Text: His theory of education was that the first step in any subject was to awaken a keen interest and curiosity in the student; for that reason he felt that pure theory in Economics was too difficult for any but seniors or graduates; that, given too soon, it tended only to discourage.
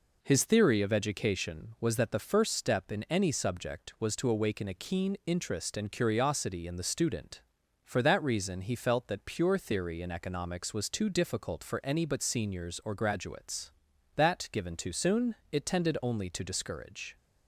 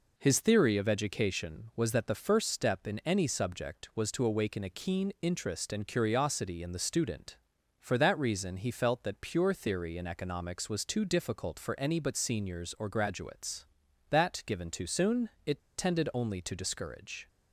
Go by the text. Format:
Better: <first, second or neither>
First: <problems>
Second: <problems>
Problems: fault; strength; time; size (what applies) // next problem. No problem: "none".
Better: first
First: none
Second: pauses between "it" and "tended"; slight; at 15.6 s; 0.17 s long